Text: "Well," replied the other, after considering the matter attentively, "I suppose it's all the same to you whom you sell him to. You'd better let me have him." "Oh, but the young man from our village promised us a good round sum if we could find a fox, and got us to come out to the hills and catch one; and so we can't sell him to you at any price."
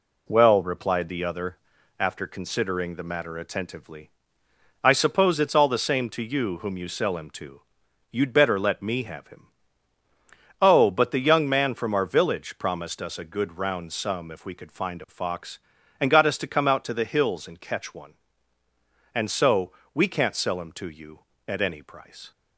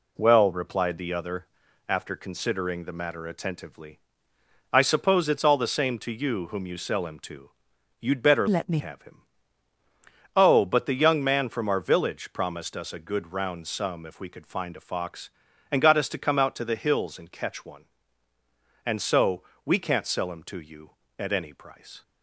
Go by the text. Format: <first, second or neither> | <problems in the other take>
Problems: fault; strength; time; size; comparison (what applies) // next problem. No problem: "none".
first | changes voice from "let" to "me"; from 8.4 to 8.7 s; 0.3 s long // pauses between "so" and "we"; slight; at 19.4 s; 0.20 s long; slight in the first